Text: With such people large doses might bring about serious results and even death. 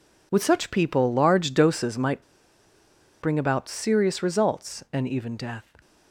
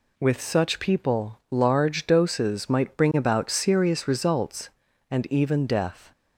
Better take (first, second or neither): second